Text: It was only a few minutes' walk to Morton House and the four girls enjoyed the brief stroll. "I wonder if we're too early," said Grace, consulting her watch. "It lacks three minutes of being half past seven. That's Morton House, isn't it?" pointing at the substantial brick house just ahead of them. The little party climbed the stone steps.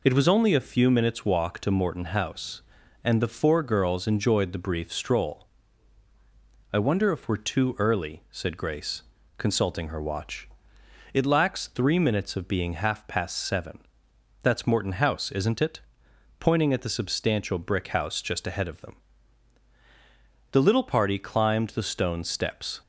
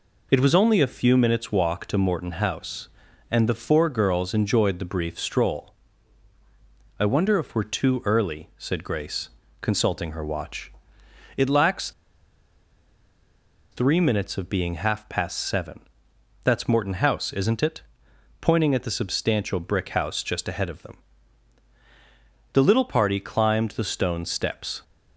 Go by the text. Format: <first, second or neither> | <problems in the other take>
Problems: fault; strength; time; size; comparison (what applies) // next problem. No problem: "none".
first | pauses between "lacks" and "three"; strong; at 11.9 s; 1.8 s long